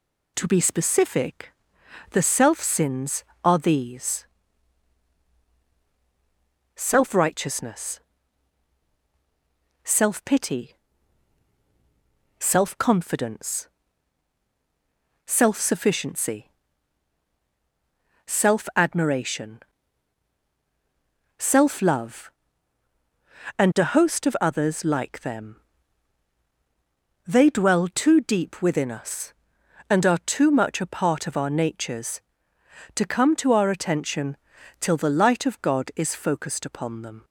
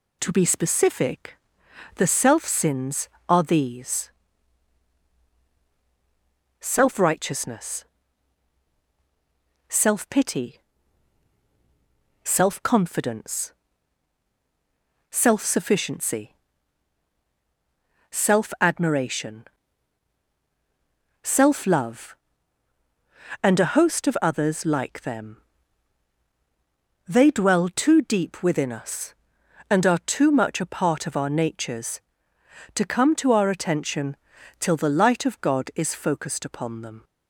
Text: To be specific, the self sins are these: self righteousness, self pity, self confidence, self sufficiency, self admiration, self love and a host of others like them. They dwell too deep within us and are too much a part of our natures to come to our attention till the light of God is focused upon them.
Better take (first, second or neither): neither